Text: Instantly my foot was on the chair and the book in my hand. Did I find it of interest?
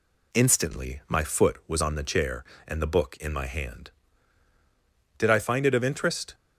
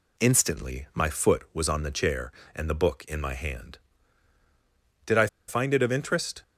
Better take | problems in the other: first | pauses between "I" and "find"; slight; at 5.2 s; 0.20 s long

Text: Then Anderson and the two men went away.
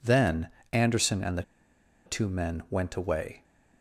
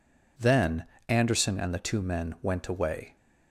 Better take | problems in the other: second | pauses between "Then" and "Anderson"; slight; at 0.4 s; 0.24 s long; slight in the second // pauses between "the" and "two"; noticeable; at 1.4 s; 0.63 s long

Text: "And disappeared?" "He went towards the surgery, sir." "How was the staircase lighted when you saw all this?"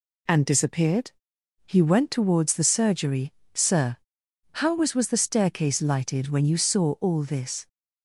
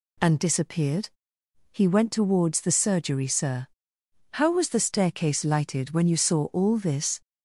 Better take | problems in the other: second | says "was" twice; at 4.9 s

